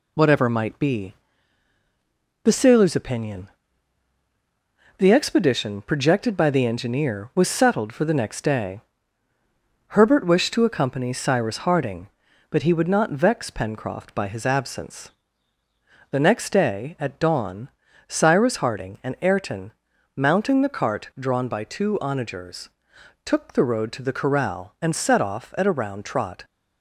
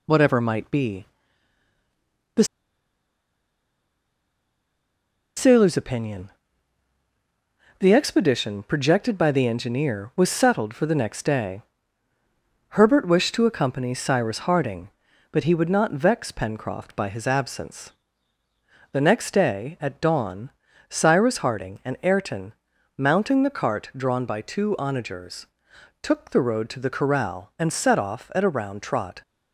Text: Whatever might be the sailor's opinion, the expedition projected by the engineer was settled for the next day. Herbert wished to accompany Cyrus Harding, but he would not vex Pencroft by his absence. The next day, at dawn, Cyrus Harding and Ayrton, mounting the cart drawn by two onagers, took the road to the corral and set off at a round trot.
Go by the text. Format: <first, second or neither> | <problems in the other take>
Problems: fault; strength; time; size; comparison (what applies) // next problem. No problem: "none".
first | pauses between "be" and "the"; strong; at 1.0 s; 1.3 s long; strong in the first // pauses between "the" and "sailor's"; strong; at 2.4 s; 2.9 s long